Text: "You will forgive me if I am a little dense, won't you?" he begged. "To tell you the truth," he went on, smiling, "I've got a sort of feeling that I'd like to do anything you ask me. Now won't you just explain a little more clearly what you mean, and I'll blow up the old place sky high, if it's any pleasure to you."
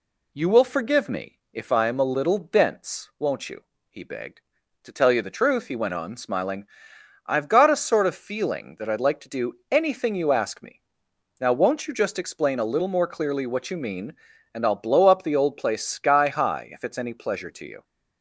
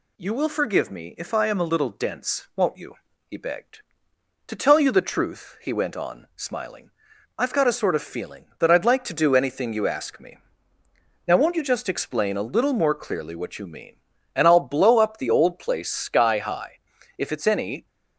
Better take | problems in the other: first | stops before "pleasure to you"; at 17.8 s

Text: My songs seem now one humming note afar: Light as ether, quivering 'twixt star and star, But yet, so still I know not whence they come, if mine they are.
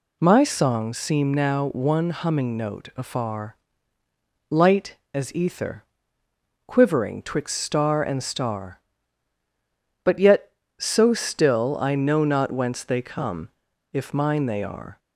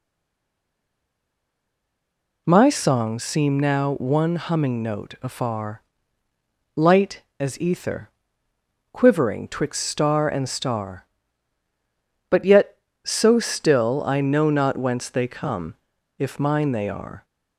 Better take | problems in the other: first | stays silent before the first word; until 2.4 s; 2.4 s long

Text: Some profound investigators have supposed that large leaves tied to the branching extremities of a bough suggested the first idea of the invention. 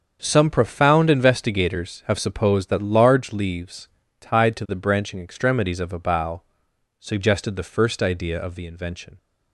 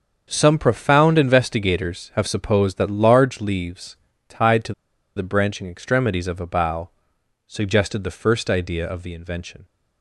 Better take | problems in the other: first | starts louder than the rest; until 1.3 s; 7 dB; also in the first // pauses between "leaves" and "tied"; slight; at 3.9 s; 0.32 s long; slight in the first // pauses between "to" and "the"; at 4.7 s; 0.43 s long // pauses between "bough" and "suggested"; noticeable; at 6.9 s; 0.54 s long; noticeable in the first

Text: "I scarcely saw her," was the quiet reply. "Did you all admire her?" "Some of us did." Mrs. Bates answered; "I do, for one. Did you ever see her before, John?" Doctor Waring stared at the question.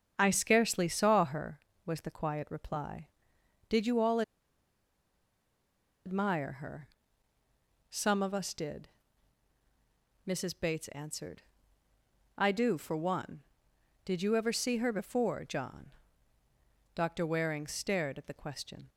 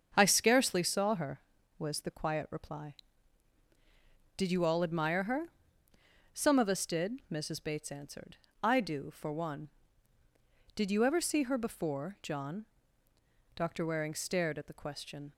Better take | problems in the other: second | starts louder than the rest; strong; until 1.2 s; 7.5 dB; strong in the second // pauses between "all" and "admire"; strong; at 4.2 s; 1.8 s long

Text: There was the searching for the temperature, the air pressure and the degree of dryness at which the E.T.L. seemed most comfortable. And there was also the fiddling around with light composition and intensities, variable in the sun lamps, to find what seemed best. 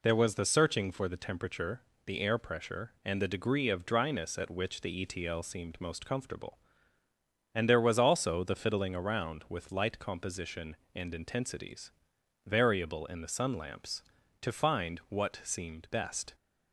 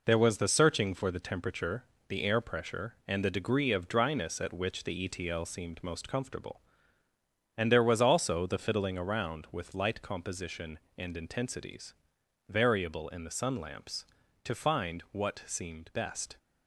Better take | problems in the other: first | gets quieter; throughout; 6 dB

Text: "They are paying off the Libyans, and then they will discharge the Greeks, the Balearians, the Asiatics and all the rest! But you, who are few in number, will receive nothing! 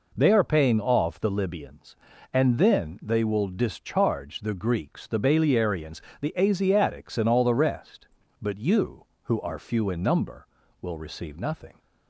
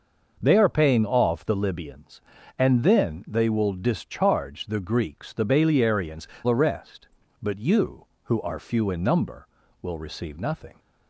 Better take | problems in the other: first | skips "the Asiatics and all"; at 6.3 s

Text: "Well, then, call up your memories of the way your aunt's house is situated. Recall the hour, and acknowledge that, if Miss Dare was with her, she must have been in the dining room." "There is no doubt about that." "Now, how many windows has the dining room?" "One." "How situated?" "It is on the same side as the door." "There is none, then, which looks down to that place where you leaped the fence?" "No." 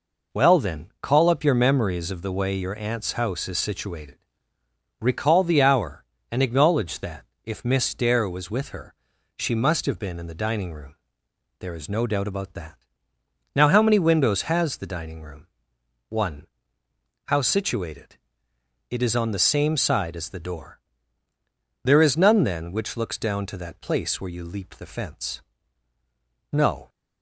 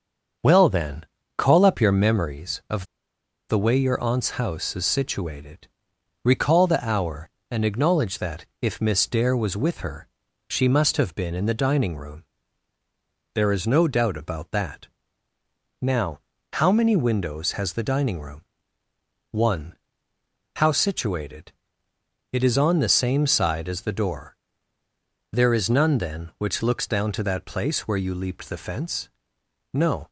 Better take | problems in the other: first | starts louder than the rest; until 1.7 s; 6.5 dB // pauses between "of" and "the"; noticeable; at 2.8 s; 0.64 s long

